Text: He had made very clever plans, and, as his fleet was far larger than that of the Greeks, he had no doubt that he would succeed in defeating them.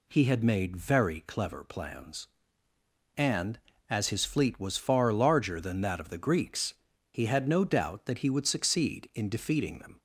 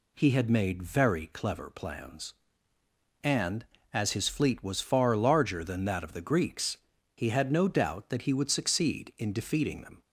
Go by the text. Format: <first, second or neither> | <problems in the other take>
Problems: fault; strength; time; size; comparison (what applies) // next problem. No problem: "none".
neither | none